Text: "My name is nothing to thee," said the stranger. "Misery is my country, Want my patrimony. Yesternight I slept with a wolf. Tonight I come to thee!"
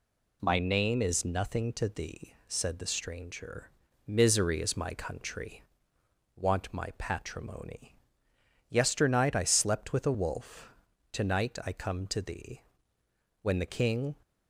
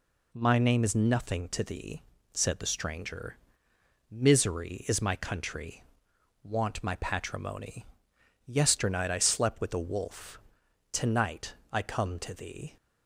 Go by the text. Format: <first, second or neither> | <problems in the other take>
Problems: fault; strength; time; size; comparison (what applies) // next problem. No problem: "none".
second | goes on to say "When the King"; noticeable; from 13.4 s on; 0.72 s long